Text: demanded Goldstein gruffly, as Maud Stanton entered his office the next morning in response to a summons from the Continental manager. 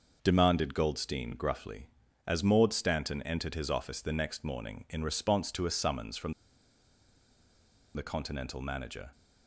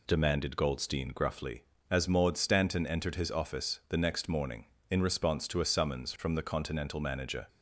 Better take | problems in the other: second | pauses between "from" and "the"; strong; at 6.3 s; 1.6 s long

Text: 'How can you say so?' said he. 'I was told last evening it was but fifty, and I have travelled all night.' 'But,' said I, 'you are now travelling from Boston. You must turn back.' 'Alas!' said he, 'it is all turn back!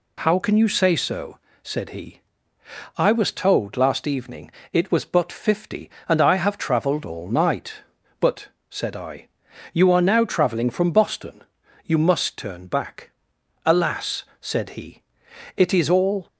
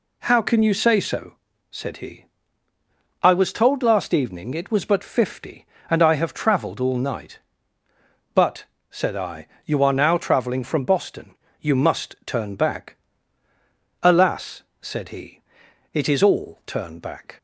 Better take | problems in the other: second | pauses between "evening" and "it"; slight; at 4.5 s; 0.22 s long // stops before "turn back"; at 16.2 s

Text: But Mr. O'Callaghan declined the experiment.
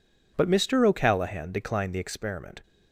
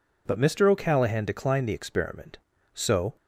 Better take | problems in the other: first | goes on to say "So"; slight; from 2.7 s on; 0.42 s long

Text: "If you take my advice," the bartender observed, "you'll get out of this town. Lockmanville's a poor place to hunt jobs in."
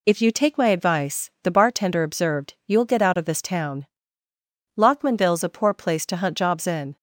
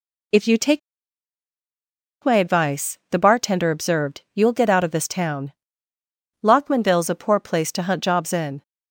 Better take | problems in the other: first | pauses between "take" and "my"; strong; at 0.7 s; 1.4 s long

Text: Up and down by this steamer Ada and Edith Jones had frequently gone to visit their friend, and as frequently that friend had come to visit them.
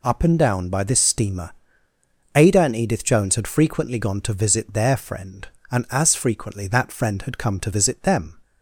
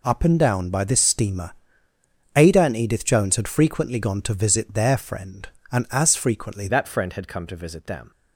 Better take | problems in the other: first | pauses between "steamer" and "Ada"; noticeable; at 1.5 s; 0.82 s long; noticeable in the first // changes voice at "that"; from 6.6 s on; 1.5 s long

